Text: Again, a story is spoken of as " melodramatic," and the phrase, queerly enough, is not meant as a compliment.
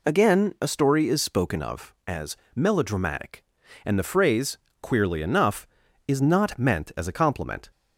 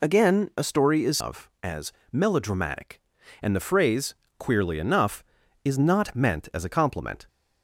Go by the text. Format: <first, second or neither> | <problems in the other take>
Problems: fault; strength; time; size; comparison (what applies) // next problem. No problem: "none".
first | skips "spoken"; at 1.1 s